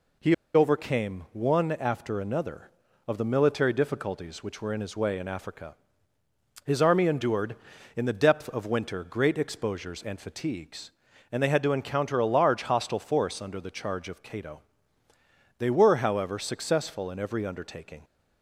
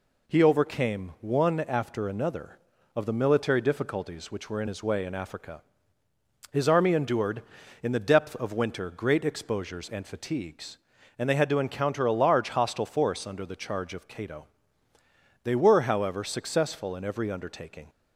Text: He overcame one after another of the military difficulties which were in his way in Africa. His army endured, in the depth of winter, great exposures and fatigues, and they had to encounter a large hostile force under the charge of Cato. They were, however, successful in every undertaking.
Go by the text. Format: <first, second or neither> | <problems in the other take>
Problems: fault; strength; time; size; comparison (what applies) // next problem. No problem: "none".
second | pauses between "He" and "overcame"; slight; at 0.3 s; 0.20 s long